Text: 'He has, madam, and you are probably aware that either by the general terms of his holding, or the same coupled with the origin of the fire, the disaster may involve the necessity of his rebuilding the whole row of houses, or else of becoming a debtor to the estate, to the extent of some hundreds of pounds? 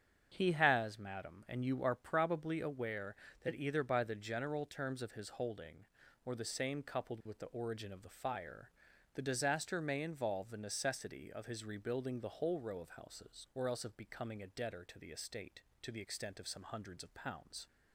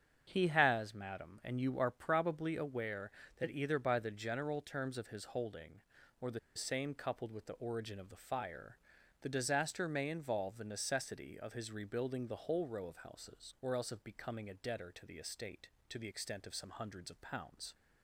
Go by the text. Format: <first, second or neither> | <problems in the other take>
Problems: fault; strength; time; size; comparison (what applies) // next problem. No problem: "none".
first | starts louder than the rest; strong; until 1.3 s; 7.5 dB; strong in the first // pauses between "the" and "same"; slight; at 6.3 s; 0.16 s long